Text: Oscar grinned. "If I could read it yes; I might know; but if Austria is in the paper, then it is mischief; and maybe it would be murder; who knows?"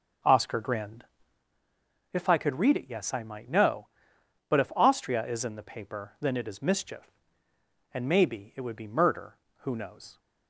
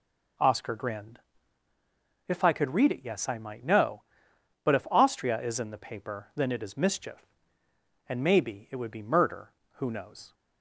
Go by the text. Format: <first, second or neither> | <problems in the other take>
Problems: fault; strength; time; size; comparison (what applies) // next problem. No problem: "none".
second | starts louder than the rest; until 1.4 s; 7 dB